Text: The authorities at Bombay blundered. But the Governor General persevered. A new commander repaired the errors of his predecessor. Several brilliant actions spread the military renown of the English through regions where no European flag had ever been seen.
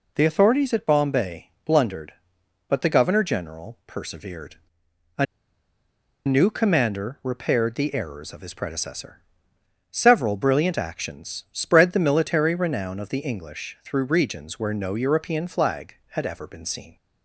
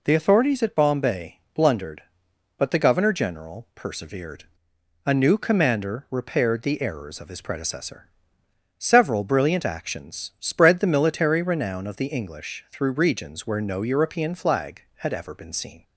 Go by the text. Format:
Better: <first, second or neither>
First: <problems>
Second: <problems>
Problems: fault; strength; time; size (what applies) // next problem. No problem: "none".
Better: second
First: pauses between "A" and "new"; at 5.2 s; 1.0 s long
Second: none